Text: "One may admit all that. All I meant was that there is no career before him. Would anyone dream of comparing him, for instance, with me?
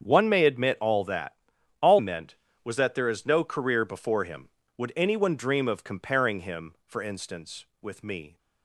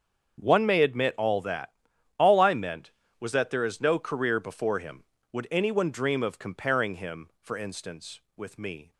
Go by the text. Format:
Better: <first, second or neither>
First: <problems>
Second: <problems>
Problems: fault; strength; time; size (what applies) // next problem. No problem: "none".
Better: second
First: starts louder than the rest; strong; until 1.0 s; 7.5 dB // skips "I"; at 1.9 s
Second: starts louder than the rest; until 1.4 s; 7 dB